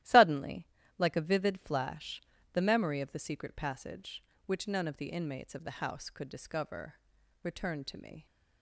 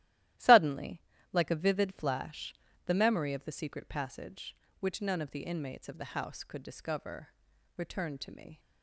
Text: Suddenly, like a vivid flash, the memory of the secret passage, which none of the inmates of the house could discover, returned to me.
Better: neither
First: starts louder than the rest; strong; until 1.3 s; 14 dB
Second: starts louder than the rest; strong; until 1.6 s; 14.5 dB

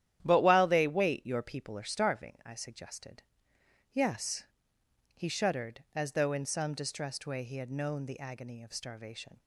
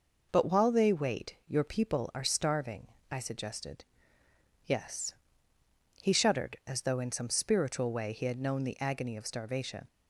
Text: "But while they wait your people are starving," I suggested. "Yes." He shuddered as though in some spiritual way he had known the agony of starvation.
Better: second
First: starts louder than the rest; strong; until 1.2 s; 11 dB // says "distressed" for "spiritual"; at 6.7 s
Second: none

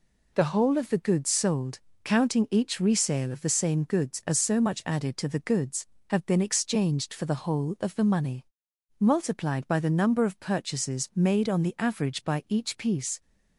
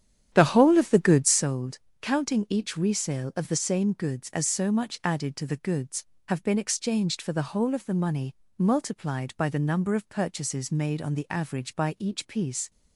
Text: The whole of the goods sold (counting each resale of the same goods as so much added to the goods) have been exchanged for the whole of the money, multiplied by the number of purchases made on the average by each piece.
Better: first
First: none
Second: starts louder than the rest; strong; until 1.5 s; 10 dB

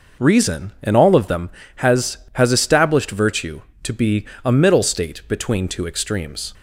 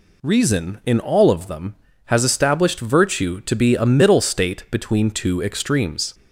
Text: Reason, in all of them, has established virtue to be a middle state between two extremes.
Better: second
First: says "has" twice; at 2.3 s // pauses between "be" and "a"; slight; at 4.2 s; 0.18 s long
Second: none

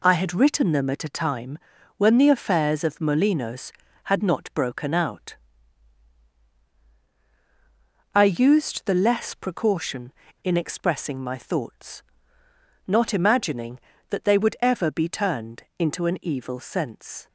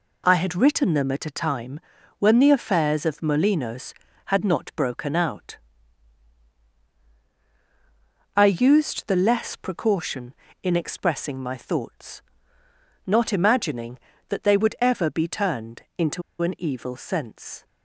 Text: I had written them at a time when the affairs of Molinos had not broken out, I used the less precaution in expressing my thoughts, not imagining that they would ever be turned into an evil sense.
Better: first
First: pauses between "time" and "when"; at 1.5 s; 0.38 s long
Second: pauses between "time" and "when"; at 1.7 s; 0.38 s long // pauses between "into" and "an"; slight; at 16.2 s; 0.20 s long

